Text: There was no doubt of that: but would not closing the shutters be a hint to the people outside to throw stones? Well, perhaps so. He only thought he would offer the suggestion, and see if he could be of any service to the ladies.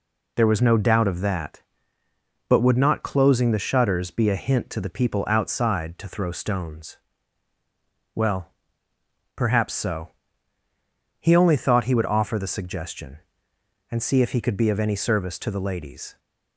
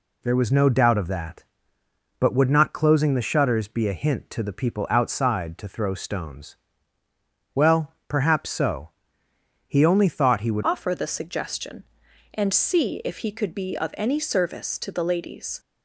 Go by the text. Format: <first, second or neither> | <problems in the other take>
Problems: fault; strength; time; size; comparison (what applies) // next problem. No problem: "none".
first | changes voice at "offer"; from 10.6 s on; 4.9 s long